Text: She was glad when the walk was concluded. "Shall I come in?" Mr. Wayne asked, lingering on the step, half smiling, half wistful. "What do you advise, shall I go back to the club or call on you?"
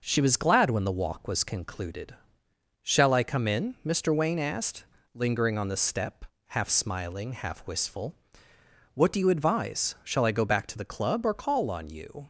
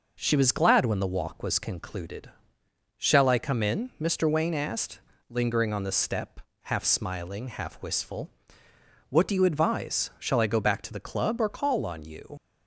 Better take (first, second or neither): first